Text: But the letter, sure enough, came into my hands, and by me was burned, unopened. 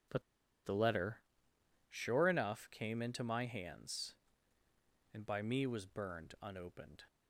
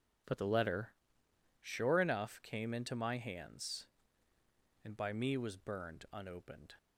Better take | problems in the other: second | pauses between "But" and "the"; at 0.2 s; 0.42 s long

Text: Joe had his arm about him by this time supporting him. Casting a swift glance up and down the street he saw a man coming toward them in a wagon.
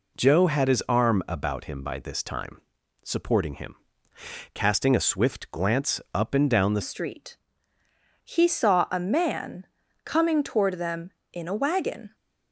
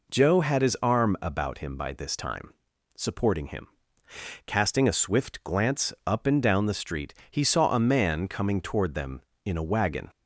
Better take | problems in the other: second | pauses between "time" and "supporting"; noticeable; at 2.5 s; 0.46 s long; noticeable in the second // changes voice at "street"; from 6.8 s on; 5.3 s long // pauses between "street" and "he"; noticeable; at 7.3 s; 0.90 s long; slight in the second // pauses between "man" and "coming"; at 9.6 s; 0.38 s long

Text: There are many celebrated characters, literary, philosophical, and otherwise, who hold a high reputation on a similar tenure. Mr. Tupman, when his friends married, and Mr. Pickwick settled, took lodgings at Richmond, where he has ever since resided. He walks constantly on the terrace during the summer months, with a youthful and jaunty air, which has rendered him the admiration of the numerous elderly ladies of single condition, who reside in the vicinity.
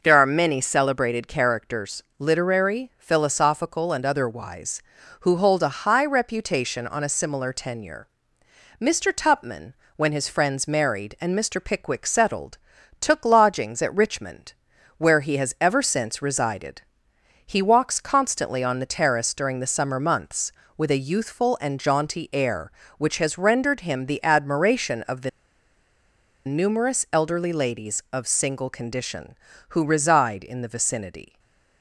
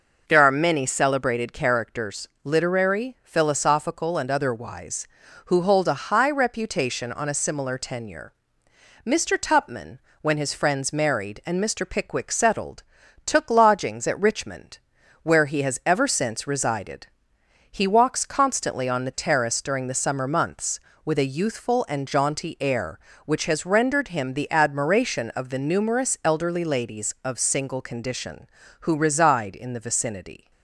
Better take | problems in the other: second | pauses between "the" and "numerous"; at 25.2 s; 1.1 s long // stays silent after the last word; slight; from 31.2 s on; 0.6 s long

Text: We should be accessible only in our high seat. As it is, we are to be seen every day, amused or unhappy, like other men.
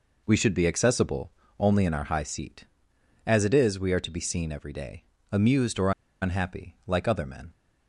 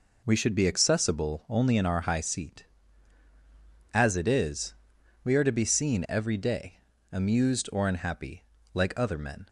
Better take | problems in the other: second | pauses between "accessible" and "only"; slight; at 1.3 s; 0.28 s long // pauses between "or" and "unhappy"; slight; at 5.9 s; 0.30 s long

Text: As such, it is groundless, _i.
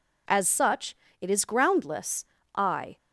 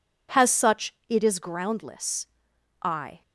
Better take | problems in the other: first | says "Has" for "As"; at 0.3 s

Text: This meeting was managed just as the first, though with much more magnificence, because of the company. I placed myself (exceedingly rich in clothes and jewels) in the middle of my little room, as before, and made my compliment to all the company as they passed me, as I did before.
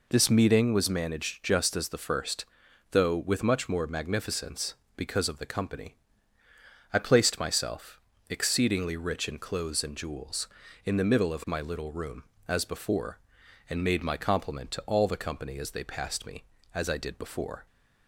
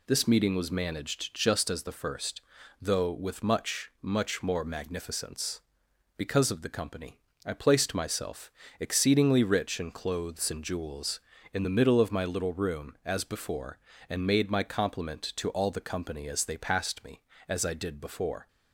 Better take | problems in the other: first | says "much" twice; at 4.0 s

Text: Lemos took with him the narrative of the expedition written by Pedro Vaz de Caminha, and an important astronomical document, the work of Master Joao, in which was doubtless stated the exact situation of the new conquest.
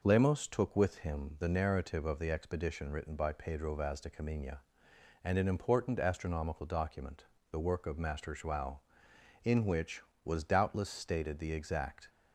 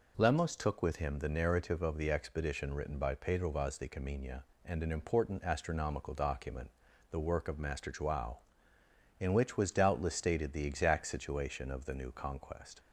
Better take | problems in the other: second | stops before "situation of the new conquest"; at 12.0 s

